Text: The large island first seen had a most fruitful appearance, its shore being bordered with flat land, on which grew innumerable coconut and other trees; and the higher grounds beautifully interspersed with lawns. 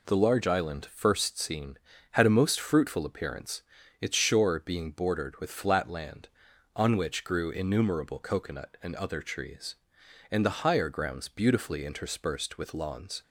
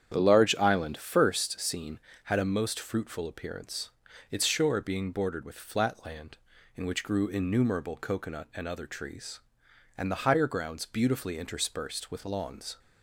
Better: first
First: none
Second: starts louder than the rest; strong; until 1.1 s; 8.5 dB // says "in" for "on"; at 6.7 s

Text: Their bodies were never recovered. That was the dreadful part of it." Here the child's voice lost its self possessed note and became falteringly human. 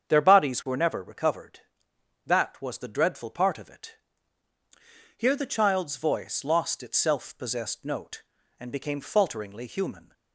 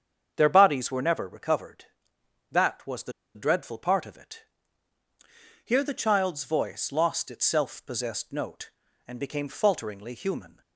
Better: first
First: starts louder than the rest; strong; until 1.1 s; 7.5 dB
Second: starts louder than the rest; strong; until 1.3 s; 7.5 dB // pauses between "the" and "dreadful"; slight; at 3.1 s; 0.22 s long

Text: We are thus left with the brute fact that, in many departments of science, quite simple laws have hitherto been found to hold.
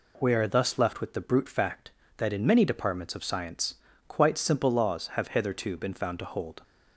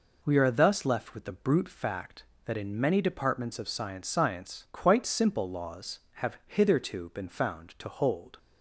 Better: first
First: none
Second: says "science" twice; at 4.0 s

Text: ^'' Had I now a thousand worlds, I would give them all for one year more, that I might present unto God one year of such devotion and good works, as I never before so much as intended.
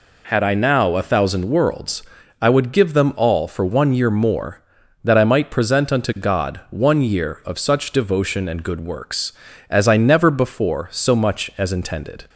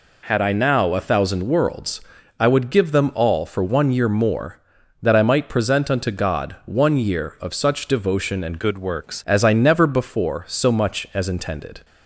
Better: first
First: none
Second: changes voice from "good" to "works"; from 8.5 to 9.2 s; 0.7 s long

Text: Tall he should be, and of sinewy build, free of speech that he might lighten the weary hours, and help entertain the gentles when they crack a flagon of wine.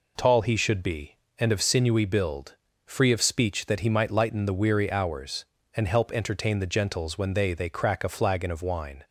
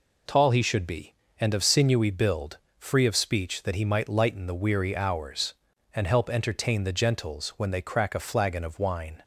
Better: second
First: says "they" twice; at 7.5 s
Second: none

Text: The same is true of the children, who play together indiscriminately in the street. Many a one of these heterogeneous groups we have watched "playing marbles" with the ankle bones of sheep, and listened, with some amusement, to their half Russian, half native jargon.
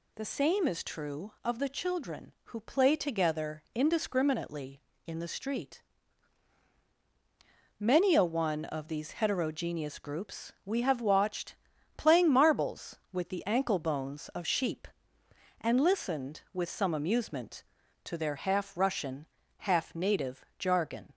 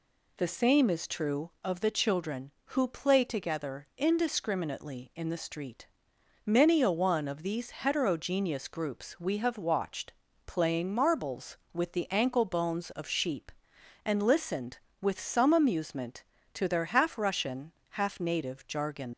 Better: first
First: pauses between "watched" and "playing"; at 11.5 s; 0.42 s long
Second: pauses between "watched" and "playing"; slight; at 10.1 s; 0.34 s long // leaves "jargon" unfinished; at 19.1 s; 100 ms

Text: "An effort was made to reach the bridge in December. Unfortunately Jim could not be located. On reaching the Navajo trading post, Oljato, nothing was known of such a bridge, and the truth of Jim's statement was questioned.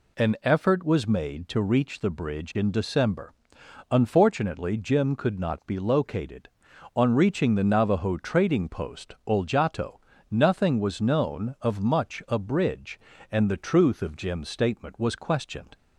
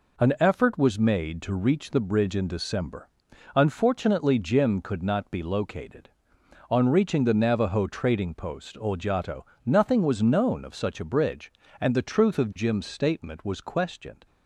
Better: second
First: says "much" for "such"; at 11.8 s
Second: none

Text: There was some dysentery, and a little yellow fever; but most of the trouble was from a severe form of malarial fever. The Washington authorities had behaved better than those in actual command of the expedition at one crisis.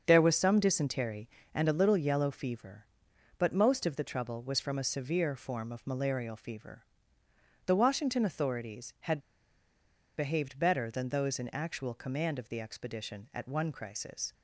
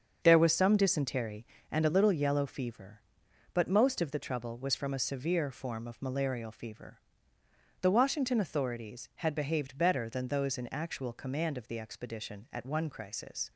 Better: second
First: starts louder than the rest; until 1.0 s; 6.5 dB // pauses between "had" and "behaved"; at 9.1 s; 0.99 s long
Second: starts louder than the rest; until 1.2 s; 6.5 dB

